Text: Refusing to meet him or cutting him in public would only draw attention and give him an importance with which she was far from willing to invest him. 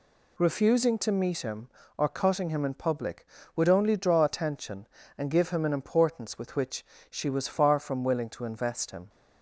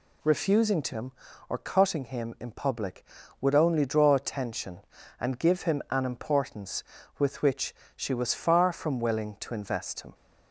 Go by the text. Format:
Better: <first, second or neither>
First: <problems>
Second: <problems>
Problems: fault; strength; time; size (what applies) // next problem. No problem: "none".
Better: first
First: pauses between "which" and "she"; slight; at 6.8 s; 0.24 s long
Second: skips "meet"; at 0.9 s // pauses between "which" and "she"; slight; at 7.7 s; 0.20 s long